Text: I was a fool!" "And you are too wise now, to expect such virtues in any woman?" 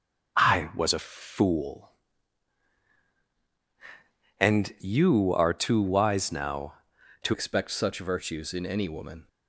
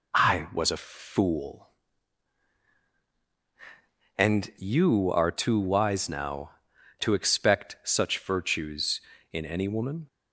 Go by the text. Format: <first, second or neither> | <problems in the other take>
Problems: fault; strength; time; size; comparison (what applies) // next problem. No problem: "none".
second | starts louder than the rest; noticeable; until 1.4 s; 6 dB // changes voice at "expect"; from 7.3 s on; 1.9 s long